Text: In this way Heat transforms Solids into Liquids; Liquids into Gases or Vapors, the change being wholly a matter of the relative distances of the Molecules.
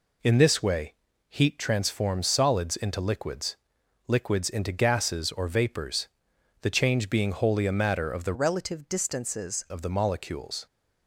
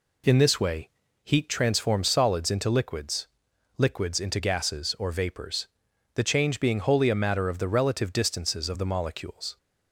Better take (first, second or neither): second